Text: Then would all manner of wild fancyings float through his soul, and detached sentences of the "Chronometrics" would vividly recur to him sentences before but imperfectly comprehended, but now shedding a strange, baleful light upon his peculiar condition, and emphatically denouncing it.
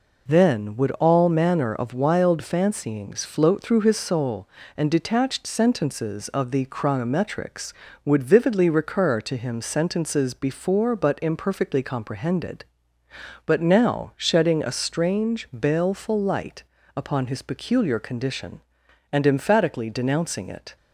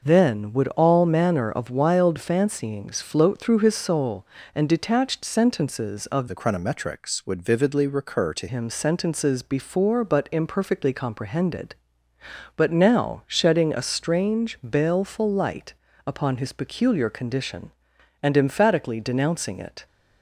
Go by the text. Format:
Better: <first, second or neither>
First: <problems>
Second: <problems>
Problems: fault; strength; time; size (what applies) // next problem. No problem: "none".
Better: first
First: pauses between "light" and "upon"; slight; at 16.6 s; 0.32 s long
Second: changes voice from "the" to "to"; from 6.2 to 8.4 s; 2.2 s long // pauses between "light" and "upon"; slight; at 15.7 s; 0.32 s long